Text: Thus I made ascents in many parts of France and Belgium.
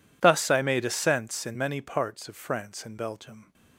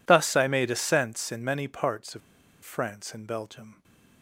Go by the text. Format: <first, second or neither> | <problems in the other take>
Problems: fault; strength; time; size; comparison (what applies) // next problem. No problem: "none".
first | pauses between "of" and "France"; at 2.2 s; 0.44 s long